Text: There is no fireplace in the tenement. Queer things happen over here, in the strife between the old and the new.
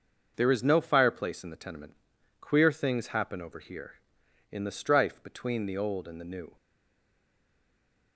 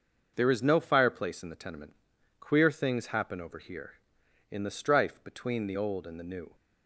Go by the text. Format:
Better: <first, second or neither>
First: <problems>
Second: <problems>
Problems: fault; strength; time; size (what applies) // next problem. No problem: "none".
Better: second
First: starts louder than the rest; noticeable; until 1.3 s; 6 dB // stays silent after the last word; noticeable; from 6.5 s on; 1.6 s long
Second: starts louder than the rest; noticeable; until 1.3 s; 6 dB